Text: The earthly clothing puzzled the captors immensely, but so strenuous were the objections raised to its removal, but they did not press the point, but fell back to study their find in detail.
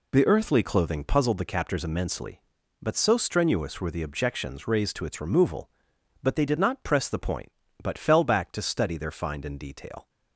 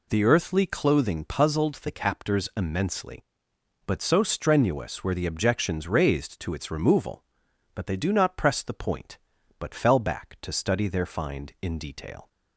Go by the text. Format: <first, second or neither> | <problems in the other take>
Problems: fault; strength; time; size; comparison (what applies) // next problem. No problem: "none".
first | says "do" for "did"; at 7.9 s